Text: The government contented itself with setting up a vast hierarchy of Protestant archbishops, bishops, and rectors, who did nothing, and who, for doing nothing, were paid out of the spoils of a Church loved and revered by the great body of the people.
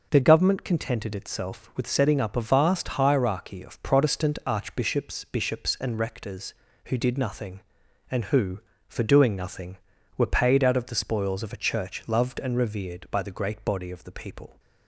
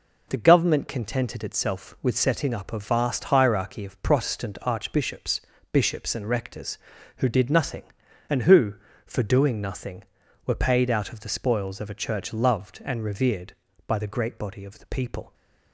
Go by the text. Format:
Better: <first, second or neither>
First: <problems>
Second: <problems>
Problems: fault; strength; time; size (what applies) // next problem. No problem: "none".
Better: neither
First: none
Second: none